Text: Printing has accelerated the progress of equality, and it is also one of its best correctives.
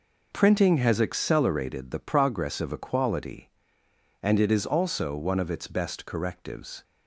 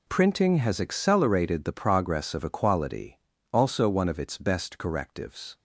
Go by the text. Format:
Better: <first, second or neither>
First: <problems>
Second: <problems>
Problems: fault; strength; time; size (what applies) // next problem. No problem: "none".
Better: first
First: none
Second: skips "and it is"; at 3.3 s